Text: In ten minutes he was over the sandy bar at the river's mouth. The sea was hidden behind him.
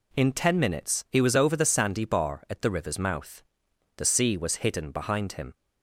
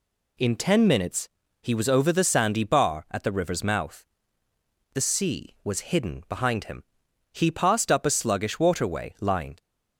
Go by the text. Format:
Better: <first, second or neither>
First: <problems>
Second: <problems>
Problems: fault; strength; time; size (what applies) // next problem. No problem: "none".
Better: first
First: none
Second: pauses between "minutes" and "he"; slight; at 1.2 s; 0.32 s long // goes on to say "He passed up a sluggish waterway lined"; strong; from 7.3 s on; 2.2 s long